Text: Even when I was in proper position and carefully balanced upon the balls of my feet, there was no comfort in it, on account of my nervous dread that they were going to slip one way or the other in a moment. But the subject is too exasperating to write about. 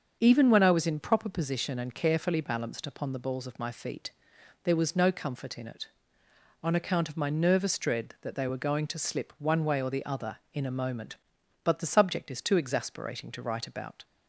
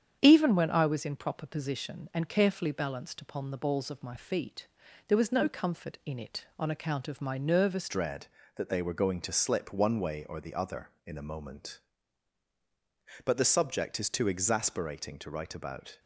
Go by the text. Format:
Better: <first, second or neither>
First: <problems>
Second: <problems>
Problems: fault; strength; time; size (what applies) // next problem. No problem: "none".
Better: first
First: starts louder than the rest; until 1.2 s; 7 dB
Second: starts louder than the rest; strong; until 1.2 s; 8 dB // changes voice at "dread"; from 7.8 s on; 8.1 s long